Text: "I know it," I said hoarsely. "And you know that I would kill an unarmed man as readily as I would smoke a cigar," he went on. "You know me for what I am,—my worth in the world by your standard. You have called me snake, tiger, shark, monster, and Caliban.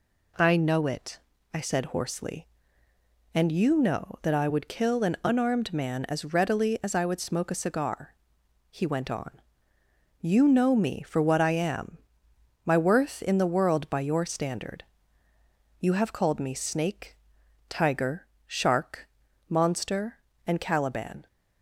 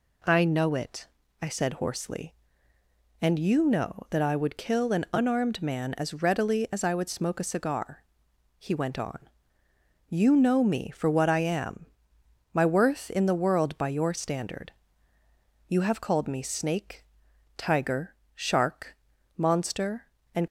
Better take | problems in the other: first | stops before "Caliban"; at 20.4 s

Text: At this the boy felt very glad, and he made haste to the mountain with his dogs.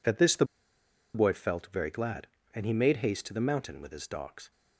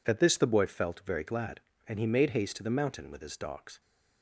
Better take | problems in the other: second | pauses between "the" and "boy"; noticeable; at 0.4 s; 0.69 s long

